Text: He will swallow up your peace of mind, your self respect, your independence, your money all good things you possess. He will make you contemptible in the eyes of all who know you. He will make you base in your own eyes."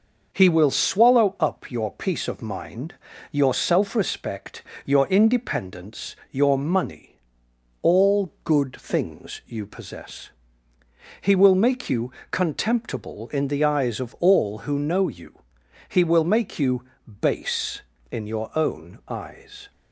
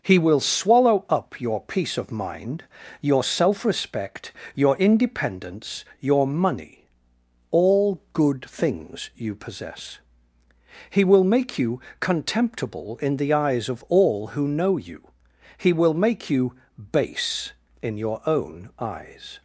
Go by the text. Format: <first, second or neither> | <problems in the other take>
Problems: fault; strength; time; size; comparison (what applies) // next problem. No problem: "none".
neither | pauses between "money" and "all"; noticeable; the same in both // pauses between "you" and "contemptible"; slight; the same in both // pauses between "you" and "base"; the same in both